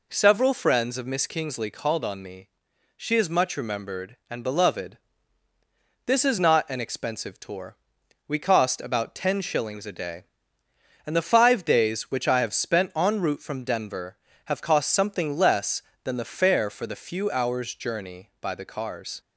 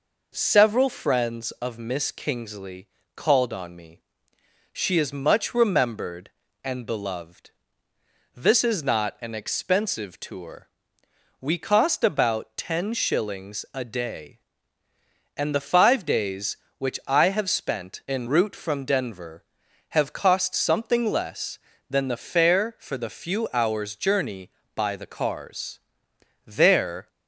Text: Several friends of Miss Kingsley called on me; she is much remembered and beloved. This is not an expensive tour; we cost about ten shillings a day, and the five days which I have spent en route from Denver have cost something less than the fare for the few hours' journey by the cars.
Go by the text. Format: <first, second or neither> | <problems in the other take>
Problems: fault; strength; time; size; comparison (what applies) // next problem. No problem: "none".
first | pauses between "Kingsley" and "called"; slight; at 2.8 s; 0.26 s long // goes on to say "There"; noticeable; from 26.4 s on; 0.62 s long